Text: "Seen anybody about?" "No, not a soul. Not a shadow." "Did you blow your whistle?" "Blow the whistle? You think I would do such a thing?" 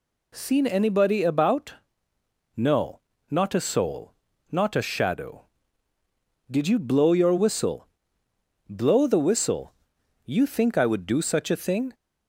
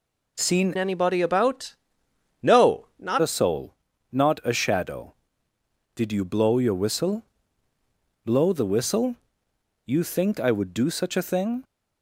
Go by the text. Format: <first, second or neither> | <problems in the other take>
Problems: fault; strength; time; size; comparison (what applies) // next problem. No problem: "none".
first | changes voice from "anybody" to "not"; from 0.7 to 3.2 s; 2.5 s long